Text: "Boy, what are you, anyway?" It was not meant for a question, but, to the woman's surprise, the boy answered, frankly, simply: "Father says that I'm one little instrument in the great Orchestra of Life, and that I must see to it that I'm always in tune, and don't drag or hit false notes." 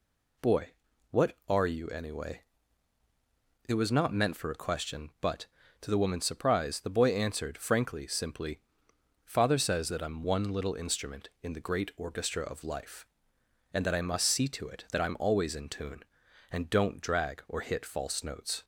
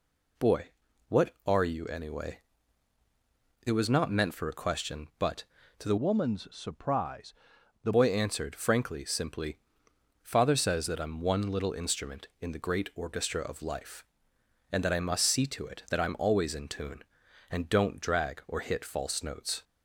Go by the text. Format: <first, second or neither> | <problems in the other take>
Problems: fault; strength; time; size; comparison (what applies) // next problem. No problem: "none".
first | changes voice from "woman's" to "the"; from 5.9 to 7.9 s; 2.0 s long